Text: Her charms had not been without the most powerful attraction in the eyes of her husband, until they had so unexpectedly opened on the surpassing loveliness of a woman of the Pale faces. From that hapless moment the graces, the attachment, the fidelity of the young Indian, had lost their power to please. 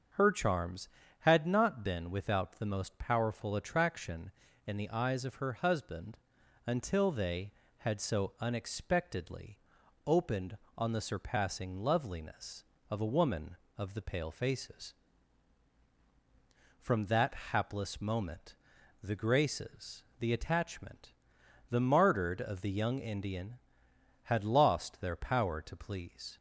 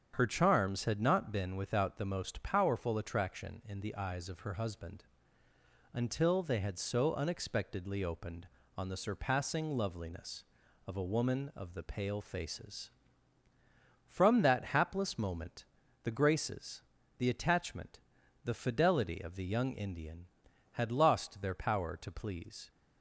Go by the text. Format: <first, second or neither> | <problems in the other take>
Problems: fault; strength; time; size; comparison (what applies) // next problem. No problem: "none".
second | starts louder than the rest; until 1.4 s; 7 dB; strong in the second // pauses between "unexpectedly" and "opened"; noticeable; at 9.5 s; 0.46 s long // pauses between "that" and "hapless"; slight; at 17.3 s; 0.16 s long // pauses between "moment" and "the"; noticeable; at 18.5 s; 0.48 s long; also in the second // says "martyred" for "fidelity"; at 21.8 s